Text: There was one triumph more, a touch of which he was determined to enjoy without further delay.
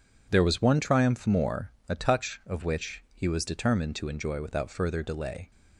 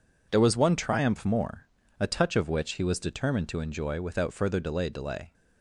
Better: first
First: none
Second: says "delay" twice; at 4.8 s

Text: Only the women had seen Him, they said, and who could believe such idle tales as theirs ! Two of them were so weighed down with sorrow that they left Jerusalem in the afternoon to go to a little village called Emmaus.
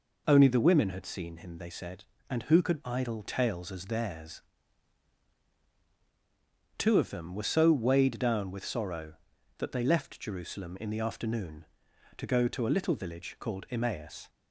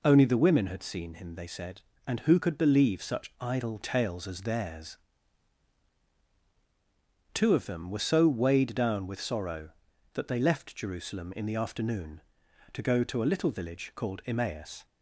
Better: second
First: skips "believe such"; at 2.8 s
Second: none

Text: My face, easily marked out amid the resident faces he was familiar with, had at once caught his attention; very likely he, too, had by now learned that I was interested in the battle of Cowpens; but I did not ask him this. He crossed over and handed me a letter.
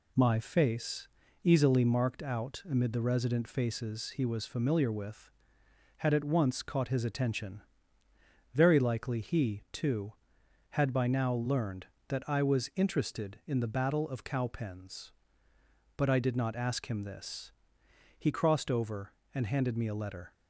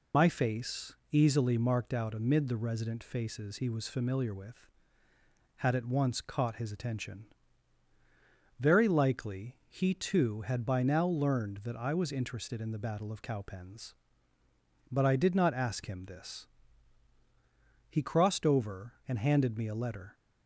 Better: first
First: none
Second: loses the start of "My"; at 0.1 s; 65 ms

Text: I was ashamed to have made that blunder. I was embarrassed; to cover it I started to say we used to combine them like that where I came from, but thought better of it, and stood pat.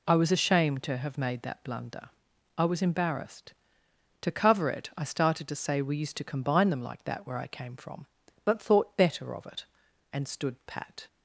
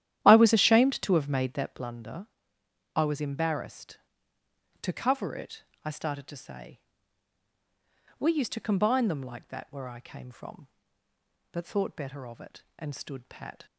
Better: first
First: none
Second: starts louder than the rest; strong; until 2.0 s; 11.5 dB // pauses between "it" and "I"; slight; at 5.6 s; 0.20 s long // pauses between "say" and "we"; strong; at 6.7 s; 1.4 s long

